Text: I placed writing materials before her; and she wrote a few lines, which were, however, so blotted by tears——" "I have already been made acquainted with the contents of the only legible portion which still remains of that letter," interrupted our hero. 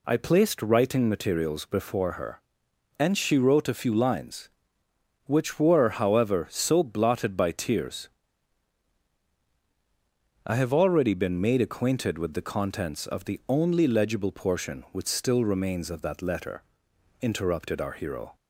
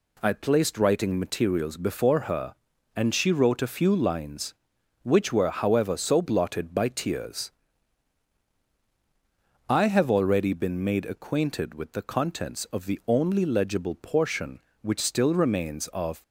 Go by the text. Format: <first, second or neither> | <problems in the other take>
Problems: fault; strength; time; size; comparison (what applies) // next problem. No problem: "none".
first | stops before "that letter interrupted our hero"; at 16.2 s